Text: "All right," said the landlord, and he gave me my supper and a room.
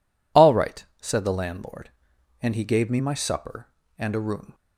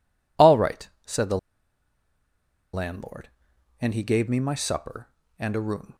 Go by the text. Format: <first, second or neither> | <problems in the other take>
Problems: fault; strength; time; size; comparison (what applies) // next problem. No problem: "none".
first | pauses between "the" and "landlord"; strong; at 1.3 s; 1.3 s long